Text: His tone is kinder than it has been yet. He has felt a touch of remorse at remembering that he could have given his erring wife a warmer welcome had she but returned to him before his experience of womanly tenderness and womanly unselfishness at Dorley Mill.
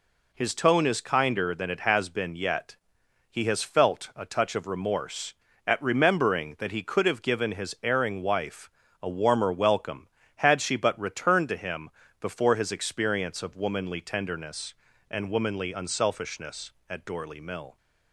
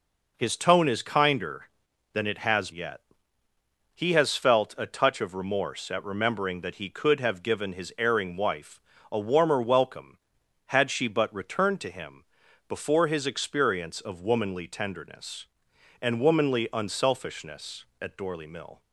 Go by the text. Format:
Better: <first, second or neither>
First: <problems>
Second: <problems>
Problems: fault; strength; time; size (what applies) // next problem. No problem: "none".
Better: first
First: pauses between "wife" and "a"; slight; at 8.7 s; 0.32 s long // pauses between "him" and "before"; slight; at 11.9 s; 0.30 s long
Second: skips "been"; at 2.7 s // pauses between "wife" and "a"; slight; at 8.8 s; 0.32 s long // pauses between "him" and "before"; at 12.2 s; 0.44 s long